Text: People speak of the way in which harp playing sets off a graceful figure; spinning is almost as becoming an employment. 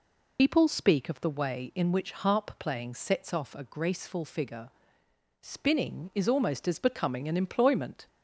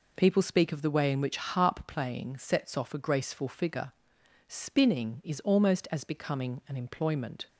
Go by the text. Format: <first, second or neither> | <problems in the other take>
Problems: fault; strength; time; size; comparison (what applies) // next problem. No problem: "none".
second | loses the start of "People"; at 0.3 s; 90 ms